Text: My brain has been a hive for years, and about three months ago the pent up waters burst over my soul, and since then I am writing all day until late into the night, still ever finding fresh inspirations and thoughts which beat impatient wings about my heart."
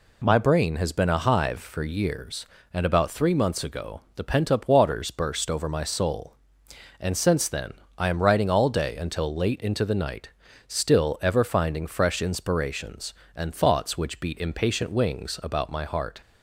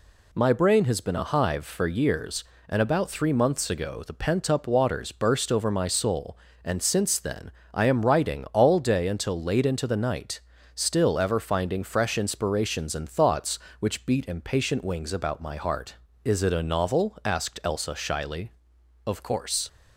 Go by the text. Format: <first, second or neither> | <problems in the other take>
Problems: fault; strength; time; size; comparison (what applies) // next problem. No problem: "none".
first | pauses between "then" and "I"; slight; at 7.5 s; 0.22 s long; slight in the first // goes on to say "Is it a novel asked Elsa shyly Of course"; strong; from 16.2 s on; 3.4 s long